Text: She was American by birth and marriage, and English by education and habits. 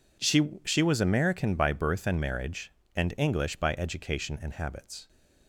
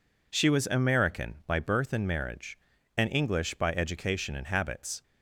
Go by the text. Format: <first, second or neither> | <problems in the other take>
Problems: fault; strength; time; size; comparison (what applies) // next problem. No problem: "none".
second | says "She" twice; at 0.6 s